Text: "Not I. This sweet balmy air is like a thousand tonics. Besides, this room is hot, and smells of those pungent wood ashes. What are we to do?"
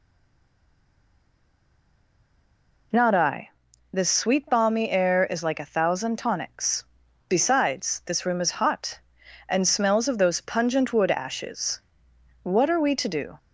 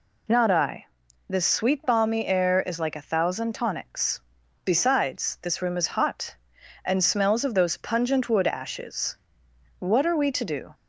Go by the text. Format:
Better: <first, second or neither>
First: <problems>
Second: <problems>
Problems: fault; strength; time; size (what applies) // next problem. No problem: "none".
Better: second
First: stays silent before the first word; strong; until 2.9 s; 2.9 s long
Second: none